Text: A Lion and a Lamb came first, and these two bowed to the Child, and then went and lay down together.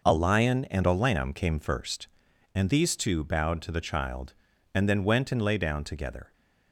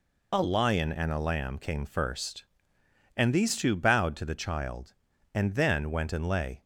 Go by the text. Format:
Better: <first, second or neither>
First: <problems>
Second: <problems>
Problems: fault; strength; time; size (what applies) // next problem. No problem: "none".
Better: first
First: none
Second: stops before "down together"; at 6.6 s